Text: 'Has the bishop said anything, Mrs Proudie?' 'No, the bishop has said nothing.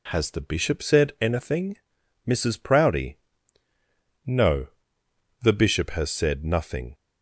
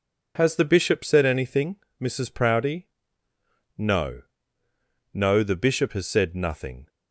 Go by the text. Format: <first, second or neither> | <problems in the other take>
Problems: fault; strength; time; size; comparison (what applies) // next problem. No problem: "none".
first | says "No" twice; at 5.1 s